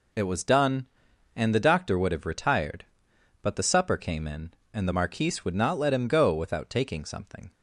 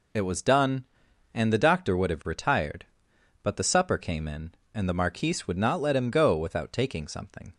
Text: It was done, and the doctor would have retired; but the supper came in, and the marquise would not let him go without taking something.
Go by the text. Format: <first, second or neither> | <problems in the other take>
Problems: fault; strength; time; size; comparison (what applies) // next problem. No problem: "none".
neither | none